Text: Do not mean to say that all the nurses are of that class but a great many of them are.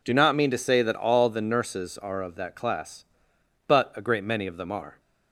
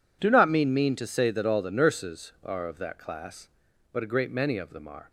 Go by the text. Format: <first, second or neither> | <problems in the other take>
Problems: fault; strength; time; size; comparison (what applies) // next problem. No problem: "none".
first | says "mean" twice; at 0.7 s